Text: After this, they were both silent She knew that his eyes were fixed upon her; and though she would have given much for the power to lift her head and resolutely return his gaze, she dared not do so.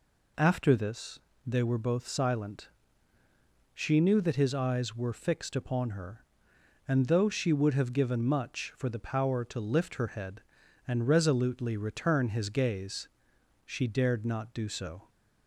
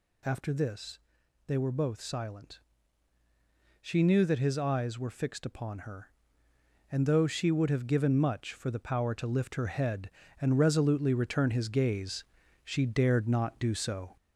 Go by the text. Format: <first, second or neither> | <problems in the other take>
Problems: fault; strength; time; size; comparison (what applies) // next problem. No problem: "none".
first | gets louder; slight; throughout; 3.5 dB // pauses between "silent" and "She"; at 2.5 s; 1.2 s long; also in the first